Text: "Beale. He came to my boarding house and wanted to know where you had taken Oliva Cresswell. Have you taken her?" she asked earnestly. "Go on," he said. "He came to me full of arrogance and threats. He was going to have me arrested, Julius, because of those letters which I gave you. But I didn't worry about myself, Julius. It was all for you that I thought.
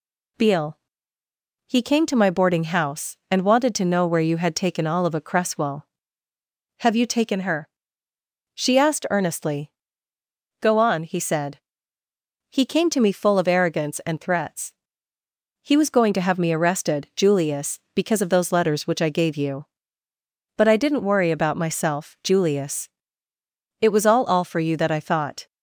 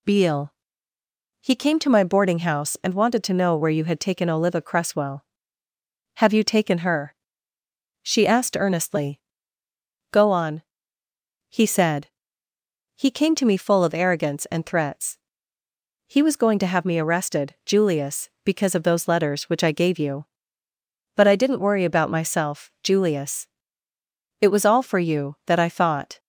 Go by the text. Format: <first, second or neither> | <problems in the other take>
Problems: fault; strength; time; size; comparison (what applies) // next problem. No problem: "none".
second | says "all" twice; at 24.2 s